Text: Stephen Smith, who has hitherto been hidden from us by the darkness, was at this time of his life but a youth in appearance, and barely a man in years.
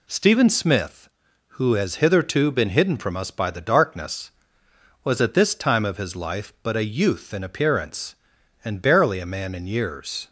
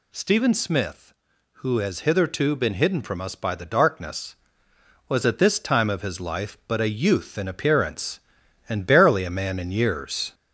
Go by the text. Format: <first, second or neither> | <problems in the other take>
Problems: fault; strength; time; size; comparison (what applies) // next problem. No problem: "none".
first | gets louder; slight; throughout; 3 dB